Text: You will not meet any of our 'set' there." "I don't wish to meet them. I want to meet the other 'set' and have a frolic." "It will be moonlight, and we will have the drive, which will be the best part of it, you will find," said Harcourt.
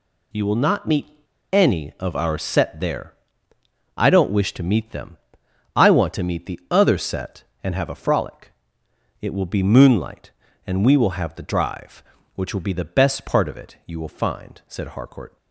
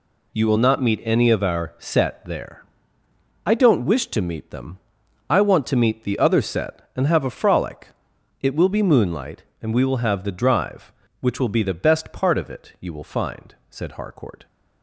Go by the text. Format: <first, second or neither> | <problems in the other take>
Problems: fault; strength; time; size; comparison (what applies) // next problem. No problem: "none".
second | pauses between "meet" and "any"; at 1.0 s; 0.43 s long